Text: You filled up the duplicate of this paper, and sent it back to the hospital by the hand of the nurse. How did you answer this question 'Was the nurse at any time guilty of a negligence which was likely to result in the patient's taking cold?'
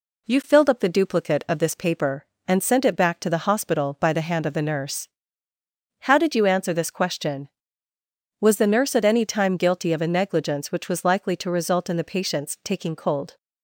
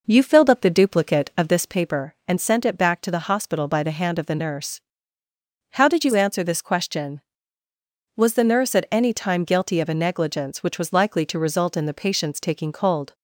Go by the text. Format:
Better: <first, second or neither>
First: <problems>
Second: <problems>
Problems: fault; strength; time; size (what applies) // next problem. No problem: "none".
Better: first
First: none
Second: starts louder than the rest; noticeable; until 1.8 s; 5 dB